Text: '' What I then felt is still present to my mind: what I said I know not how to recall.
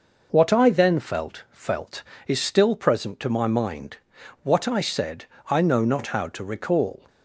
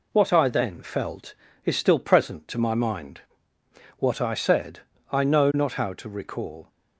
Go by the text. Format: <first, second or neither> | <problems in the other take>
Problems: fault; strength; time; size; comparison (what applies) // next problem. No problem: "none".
second | says "felt" twice; at 1.5 s // pauses between "said" and "I"; slight; at 5.2 s; 0.24 s long; slight in the second